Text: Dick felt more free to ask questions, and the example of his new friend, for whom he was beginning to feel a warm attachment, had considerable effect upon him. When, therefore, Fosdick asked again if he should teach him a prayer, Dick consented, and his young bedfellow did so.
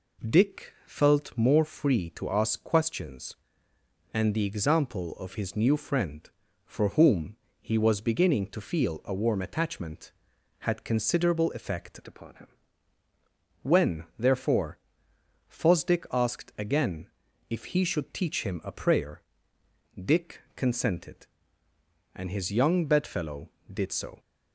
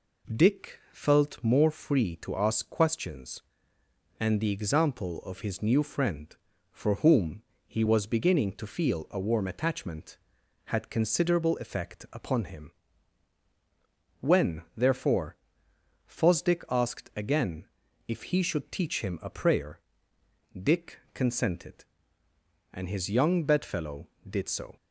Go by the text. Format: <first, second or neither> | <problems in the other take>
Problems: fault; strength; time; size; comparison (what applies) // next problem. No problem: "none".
second | pauses between "whom" and "he"; slight; at 7.3 s; 0.26 s long; slight in the second // changes voice from "upon" to "him"; from 12.0 to 12.4 s; 0.4 s long // pauses between "again" and "if"; at 17.0 s; 0.42 s long; also in the second // pauses between "Dick" and "consented"; slight; at 20.3 s; 0.16 s long; slight in the second